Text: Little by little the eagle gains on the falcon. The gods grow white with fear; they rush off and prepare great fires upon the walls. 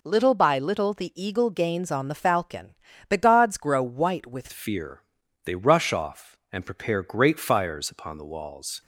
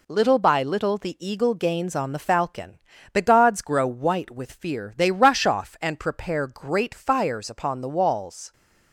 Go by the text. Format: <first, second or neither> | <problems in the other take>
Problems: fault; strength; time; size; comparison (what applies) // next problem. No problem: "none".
second | changes voice at "fear"; from 4.5 s on; 4.3 s long